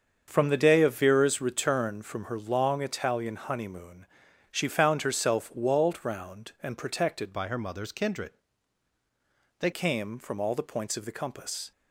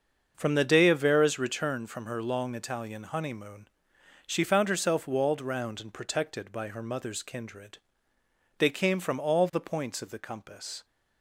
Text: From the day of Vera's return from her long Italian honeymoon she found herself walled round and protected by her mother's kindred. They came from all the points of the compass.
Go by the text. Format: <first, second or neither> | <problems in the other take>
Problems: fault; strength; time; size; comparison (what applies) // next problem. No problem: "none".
second | starts louder than the rest; until 1.2 s; 7 dB; also in the second // pauses between "honeymoon" and "she"; noticeable; at 4.0 s; 0.46 s long; noticeable in the second // changes voice from "by" to "They"; from 7.3 to 9.7 s; 2.4 s long